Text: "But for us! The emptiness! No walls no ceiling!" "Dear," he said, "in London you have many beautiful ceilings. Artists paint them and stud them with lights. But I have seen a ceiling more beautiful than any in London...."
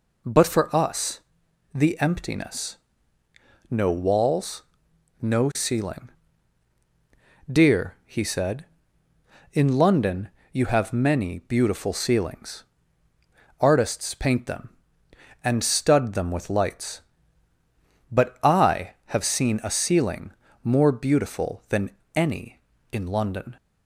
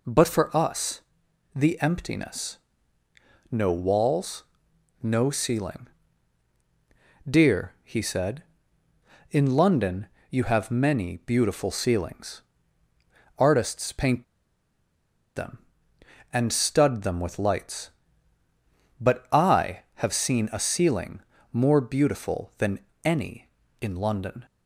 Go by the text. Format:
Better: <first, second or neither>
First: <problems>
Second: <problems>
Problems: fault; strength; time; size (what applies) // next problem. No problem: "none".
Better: first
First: pauses between "walls" and "no"; noticeable; at 4.6 s; 0.58 s long // pauses between "London" and "you"; slight; at 10.3 s; 0.22 s long // pauses between "ceiling" and "more"; slight; at 20.3 s; 0.30 s long // pauses between "than" and "any"; slight; at 21.9 s; 0.24 s long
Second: pauses between "walls" and "no"; noticeable; at 4.4 s; 0.58 s long // pauses between "London" and "you"; slight; at 10.0 s; 0.22 s long // pauses between "paint" and "them"; at 14.2 s; 1.1 s long // pauses between "ceiling" and "more"; slight; at 21.2 s; 0.30 s long // pauses between "than" and "any"; slight; at 22.7 s; 0.24 s long